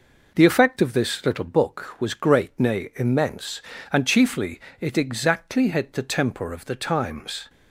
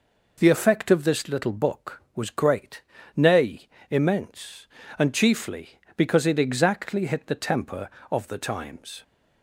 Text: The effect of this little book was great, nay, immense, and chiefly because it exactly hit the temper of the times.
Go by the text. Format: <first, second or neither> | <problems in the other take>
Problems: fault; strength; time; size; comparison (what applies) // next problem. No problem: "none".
second | skips "because"; at 4.7 s